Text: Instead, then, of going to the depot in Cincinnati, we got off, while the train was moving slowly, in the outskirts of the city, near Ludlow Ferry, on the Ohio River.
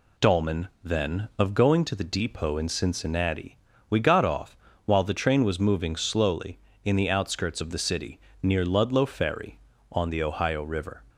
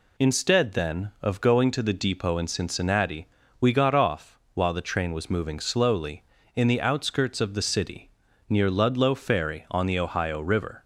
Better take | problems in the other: second | says "Dolman" for "Instead"; at 0.1 s

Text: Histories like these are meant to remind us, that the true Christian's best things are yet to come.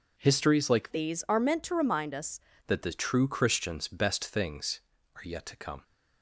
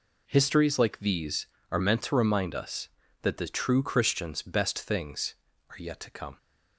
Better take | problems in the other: second | changes voice from "these" to "us"; from 0.9 to 2.3 s; 1.4 s long

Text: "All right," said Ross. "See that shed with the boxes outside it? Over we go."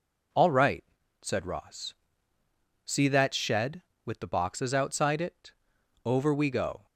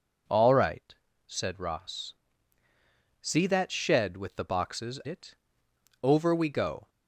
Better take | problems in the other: first | skips "outside"; at 5.0 s

